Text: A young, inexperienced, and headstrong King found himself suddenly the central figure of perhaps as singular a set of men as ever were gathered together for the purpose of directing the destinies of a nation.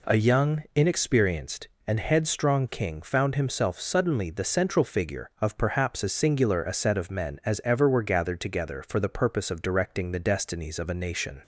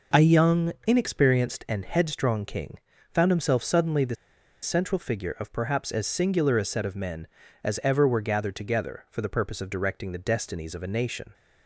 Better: first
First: none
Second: pauses between "King" and "found"; slight; at 2.7 s; 0.36 s long // pauses between "the" and "central"; noticeable; at 4.1 s; 0.48 s long

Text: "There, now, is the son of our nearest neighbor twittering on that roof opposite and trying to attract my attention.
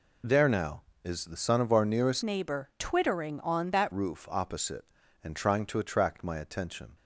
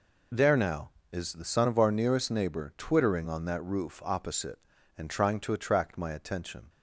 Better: second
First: changes voice from "neighbor" to "that"; from 2.2 to 3.9 s; 1.7 s long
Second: none

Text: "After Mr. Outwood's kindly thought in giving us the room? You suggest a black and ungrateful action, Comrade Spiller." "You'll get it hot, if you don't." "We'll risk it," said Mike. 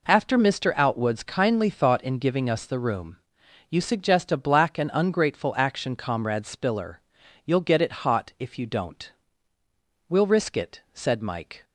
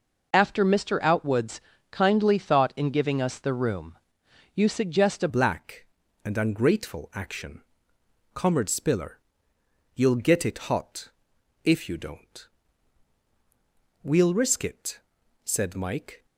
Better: first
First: none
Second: pauses between "Outwood's" and "kindly"; slight; at 1.6 s; 0.32 s long // changes voice at "black"; from 5.2 s on; 11.0 s long

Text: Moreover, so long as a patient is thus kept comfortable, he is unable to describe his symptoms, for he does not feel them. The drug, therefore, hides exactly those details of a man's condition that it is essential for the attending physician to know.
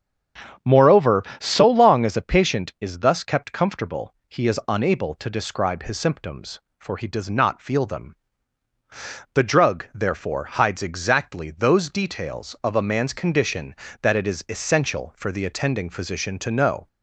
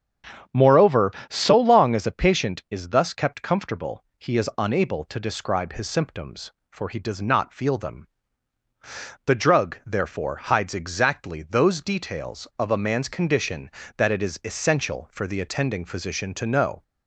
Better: neither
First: starts louder than the rest; strong; until 1.8 s; 8 dB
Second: starts louder than the rest; strong; until 1.7 s; 8 dB

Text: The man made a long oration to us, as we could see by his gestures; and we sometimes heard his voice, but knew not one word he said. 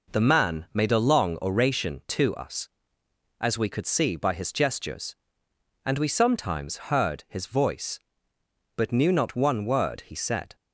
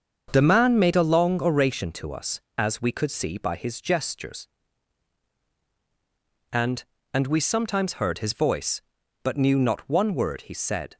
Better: first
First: none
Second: starts louder than the rest; until 1.3 s; 7 dB // says "and" twice; at 7.1 s

